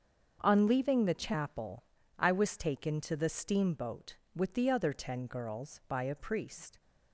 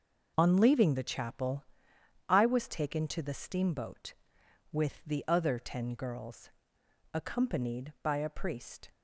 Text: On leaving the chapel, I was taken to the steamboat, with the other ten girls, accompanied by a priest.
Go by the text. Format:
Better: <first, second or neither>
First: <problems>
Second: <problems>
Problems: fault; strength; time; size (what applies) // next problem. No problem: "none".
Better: second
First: starts louder than the rest; until 1.4 s; 7 dB // skips "accompanied"; at 5.8 s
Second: none